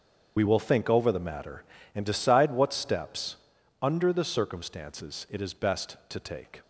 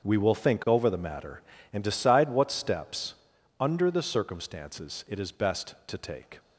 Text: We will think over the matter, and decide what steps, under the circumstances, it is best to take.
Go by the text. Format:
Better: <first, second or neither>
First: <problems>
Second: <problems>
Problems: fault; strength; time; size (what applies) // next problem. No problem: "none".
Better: second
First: loses the start of "We"; at 0.3 s; 65 ms // starts louder than the rest; strong; until 1.3 s; 7 dB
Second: starts louder than the rest; until 1.0 s; 6.5 dB